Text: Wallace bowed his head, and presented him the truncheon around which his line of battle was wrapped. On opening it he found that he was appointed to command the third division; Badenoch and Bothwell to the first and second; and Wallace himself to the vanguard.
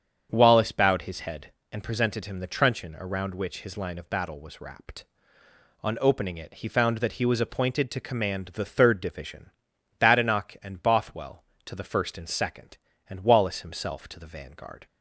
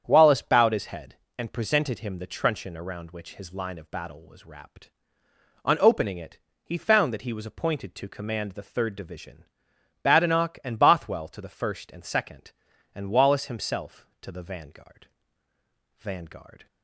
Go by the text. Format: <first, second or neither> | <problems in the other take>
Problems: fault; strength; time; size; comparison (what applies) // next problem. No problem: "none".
first | starts louder than the rest; strong; until 1.0 s; 8.5 dB; strong in the first // pauses between "it" and "he"; slight; at 6.3 s; 0.24 s long // says "vanguard" twice; at 15.9 s